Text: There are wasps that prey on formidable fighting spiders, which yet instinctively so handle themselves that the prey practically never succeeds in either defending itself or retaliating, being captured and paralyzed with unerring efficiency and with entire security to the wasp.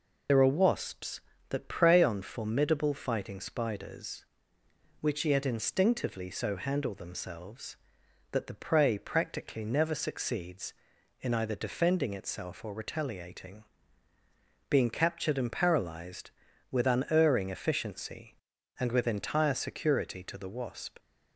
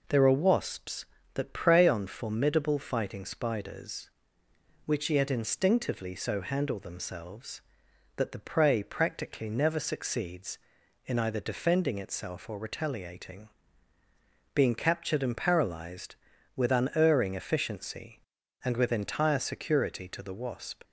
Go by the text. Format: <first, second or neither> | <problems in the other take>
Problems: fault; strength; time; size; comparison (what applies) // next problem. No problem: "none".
second | loses the start of "There"; at 0.2 s; 95 ms